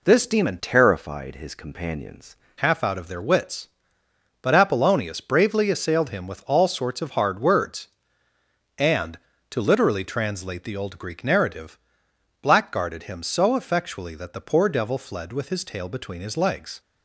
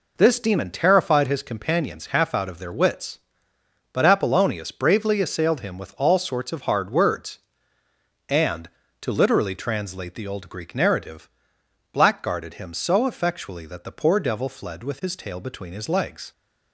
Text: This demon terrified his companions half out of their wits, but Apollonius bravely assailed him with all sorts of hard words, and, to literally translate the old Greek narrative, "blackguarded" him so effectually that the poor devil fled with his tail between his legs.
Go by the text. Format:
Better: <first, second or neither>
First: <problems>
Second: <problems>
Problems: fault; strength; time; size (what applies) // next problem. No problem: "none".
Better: second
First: changes voice from "terrified" to "companions"; from 0.6 to 2.3 s; 1.7 s long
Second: none